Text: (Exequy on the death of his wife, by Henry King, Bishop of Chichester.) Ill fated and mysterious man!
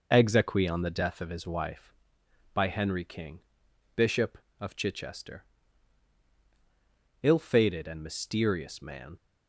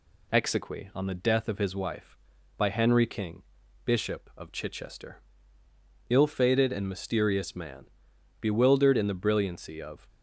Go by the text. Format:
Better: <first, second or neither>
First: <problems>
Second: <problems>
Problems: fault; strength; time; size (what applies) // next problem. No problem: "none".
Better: first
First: none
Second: goes on to say "bewildered in the brilliancy of"; strong; from 8.3 s on; 1.6 s long